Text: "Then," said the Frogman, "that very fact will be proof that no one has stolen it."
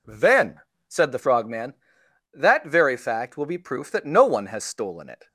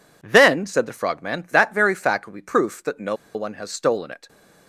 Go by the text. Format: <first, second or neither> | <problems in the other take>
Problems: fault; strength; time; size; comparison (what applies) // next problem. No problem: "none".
first | pauses between "no" and "one"; slight; at 3.1 s; 0.19 s long